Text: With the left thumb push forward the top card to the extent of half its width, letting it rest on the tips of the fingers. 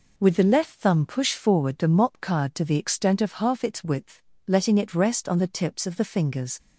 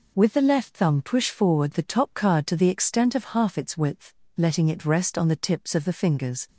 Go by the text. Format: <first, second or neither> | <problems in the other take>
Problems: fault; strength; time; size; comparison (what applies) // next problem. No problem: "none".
second | says "mop" for "top"; at 1.8 s